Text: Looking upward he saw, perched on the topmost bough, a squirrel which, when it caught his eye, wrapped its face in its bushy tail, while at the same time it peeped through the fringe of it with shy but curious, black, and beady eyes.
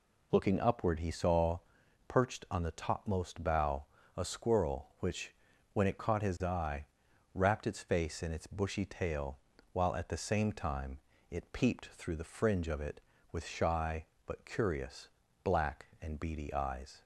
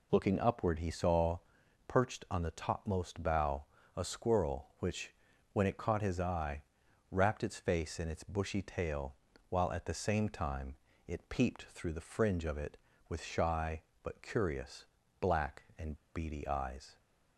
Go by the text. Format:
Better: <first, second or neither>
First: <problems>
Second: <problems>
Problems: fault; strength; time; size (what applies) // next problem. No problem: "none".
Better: first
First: pauses between "time" and "it"; slight; at 10.9 s; 0.30 s long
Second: pauses between "time" and "it"; slight; at 10.7 s; 0.30 s long // pauses between "and" and "beady"; slight; at 15.9 s; 0.18 s long